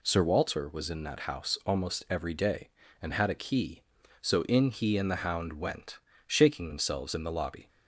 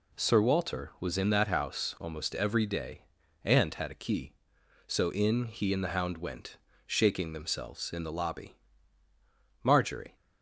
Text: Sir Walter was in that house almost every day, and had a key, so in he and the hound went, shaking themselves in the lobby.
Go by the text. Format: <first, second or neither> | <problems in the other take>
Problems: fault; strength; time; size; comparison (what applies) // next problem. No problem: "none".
first | goes on to say "Marjorie"; from 9.6 s on; 0.54 s long